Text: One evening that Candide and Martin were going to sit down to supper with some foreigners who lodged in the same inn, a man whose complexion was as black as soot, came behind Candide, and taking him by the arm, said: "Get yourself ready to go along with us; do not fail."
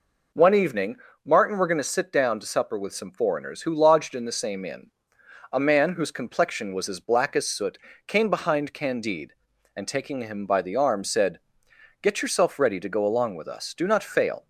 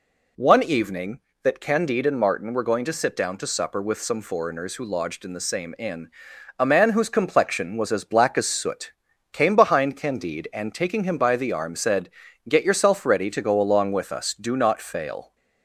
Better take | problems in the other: second | skips "that Candide and"; at 1.1 s

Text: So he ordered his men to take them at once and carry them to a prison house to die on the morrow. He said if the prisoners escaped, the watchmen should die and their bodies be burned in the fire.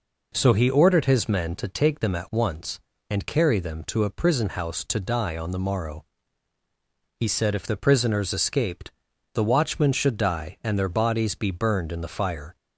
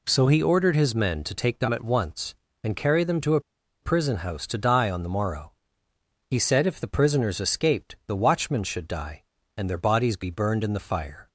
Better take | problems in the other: first | pauses between "a" and "prison"; at 3.4 s; 0.42 s long

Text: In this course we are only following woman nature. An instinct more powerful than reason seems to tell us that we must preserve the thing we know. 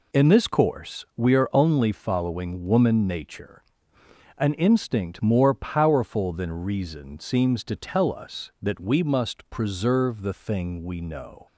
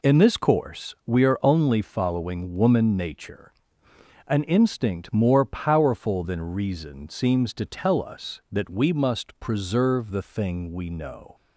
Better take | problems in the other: neither | none

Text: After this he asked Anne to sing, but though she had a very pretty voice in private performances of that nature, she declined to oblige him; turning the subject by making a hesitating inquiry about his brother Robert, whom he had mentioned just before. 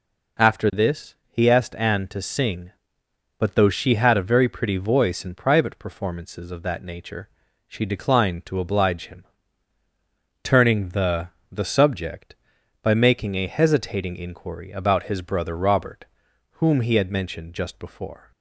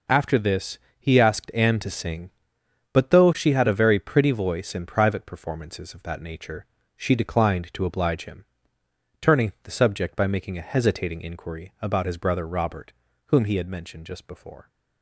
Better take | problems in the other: second | pauses between "this" and "he"; slight; at 1.1 s; 0.16 s long; slight in the second // says "the" twice; at 11.5 s

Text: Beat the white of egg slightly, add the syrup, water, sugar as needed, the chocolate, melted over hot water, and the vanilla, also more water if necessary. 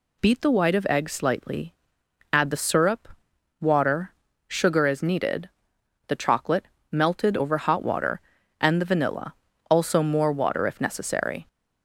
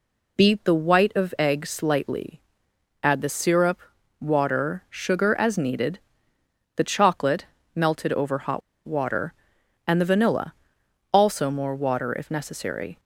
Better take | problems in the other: first | pauses between "hot" and "water"; slight; at 8.6 s; 0.24 s long

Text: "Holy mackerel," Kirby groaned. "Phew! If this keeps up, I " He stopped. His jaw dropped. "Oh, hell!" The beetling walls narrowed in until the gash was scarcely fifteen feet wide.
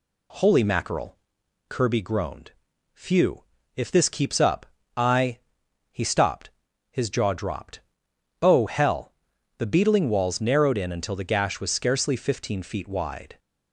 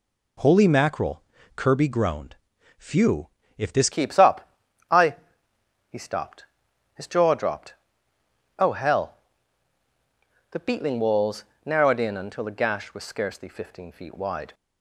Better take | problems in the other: first | changes voice at "keeps"; from 3.9 s on; 10.6 s long // pauses between "walls" and "narrowed"; slight; at 11.4 s; 0.22 s long

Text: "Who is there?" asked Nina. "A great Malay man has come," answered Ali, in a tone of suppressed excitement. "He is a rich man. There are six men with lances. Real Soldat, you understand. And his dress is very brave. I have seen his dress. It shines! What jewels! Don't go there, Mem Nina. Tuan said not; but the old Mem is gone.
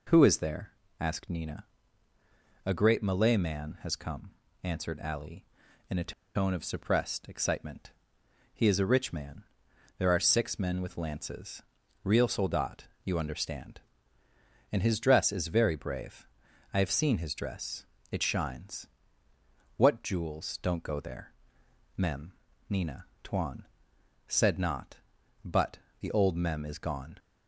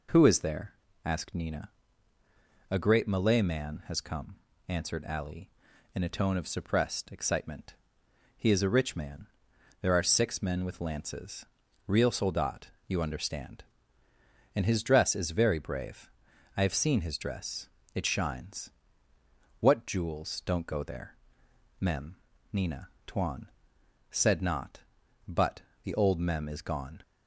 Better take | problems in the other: second | pauses between "a" and "tone"; slight; at 6.1 s; 0.21 s long // pauses between "Mem" and "Nina"; slight; at 22.3 s; 0.36 s long; slight in the second // pauses between "Tuan" and "said"; noticeable; at 23.6 s; 0.62 s long; noticeable in the second // pauses between "but" and "the"; slight; at 25.7 s; 0.22 s long; slight in the second

